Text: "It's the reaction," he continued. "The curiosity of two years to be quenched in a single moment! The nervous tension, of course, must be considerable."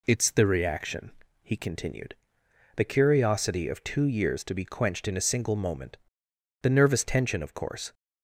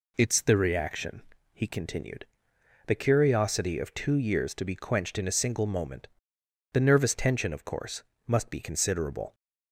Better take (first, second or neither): second